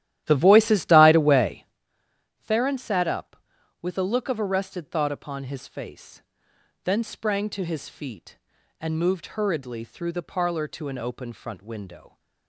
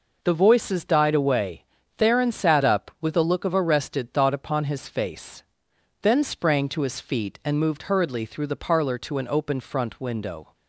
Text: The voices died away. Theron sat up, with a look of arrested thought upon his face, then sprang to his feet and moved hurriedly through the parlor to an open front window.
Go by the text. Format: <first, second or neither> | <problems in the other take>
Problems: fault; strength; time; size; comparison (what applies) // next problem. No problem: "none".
second | starts louder than the rest; strong; until 1.9 s; 12.5 dB